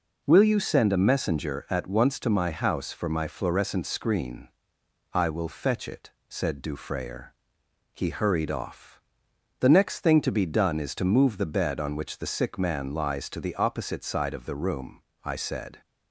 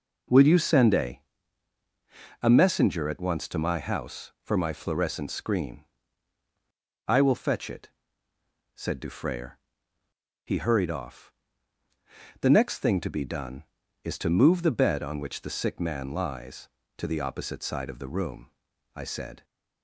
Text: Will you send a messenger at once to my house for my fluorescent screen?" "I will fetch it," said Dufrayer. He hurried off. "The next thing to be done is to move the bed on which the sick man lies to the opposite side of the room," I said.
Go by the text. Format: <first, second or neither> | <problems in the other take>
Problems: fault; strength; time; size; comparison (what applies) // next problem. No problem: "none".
first | says "a" twice; at 2.4 s